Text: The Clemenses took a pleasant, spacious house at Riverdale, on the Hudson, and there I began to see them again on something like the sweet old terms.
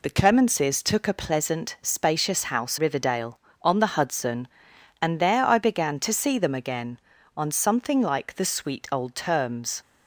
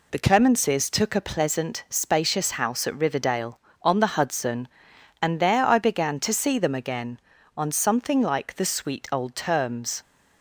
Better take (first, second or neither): second